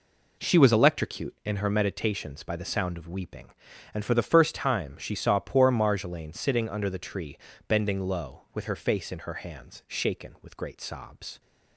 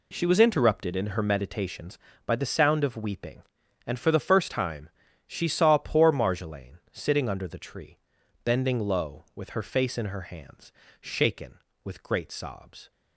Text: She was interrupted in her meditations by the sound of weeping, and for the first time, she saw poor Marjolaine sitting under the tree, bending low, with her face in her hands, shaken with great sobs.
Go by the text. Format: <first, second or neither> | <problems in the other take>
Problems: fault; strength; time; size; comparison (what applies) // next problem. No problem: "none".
second | says "electrocute" for "interrupted"; at 0.7 s